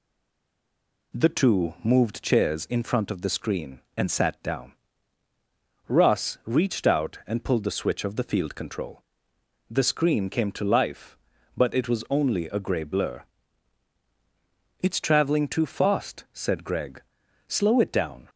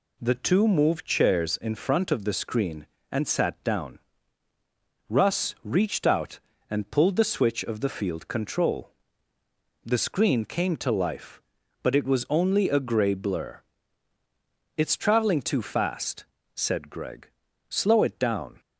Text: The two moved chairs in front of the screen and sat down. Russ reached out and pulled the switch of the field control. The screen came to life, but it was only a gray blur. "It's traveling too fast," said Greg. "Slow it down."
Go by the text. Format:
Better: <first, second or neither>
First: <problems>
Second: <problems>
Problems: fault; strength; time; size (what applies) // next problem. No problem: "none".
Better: second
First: stays silent before the first word; until 1.1 s; 1.1 s long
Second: none